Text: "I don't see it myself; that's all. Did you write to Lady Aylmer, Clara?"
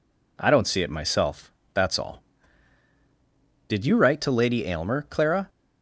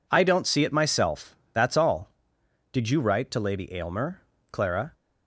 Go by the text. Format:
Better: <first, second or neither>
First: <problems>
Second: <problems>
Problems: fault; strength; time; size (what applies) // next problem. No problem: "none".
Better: neither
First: none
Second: none